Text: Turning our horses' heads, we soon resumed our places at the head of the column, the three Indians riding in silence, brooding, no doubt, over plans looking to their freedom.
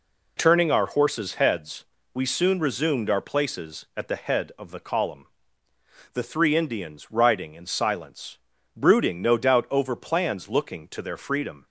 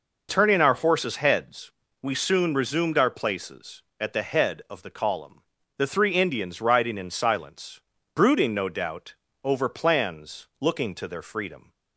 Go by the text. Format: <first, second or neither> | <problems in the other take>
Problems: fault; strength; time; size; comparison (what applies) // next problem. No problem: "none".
neither | none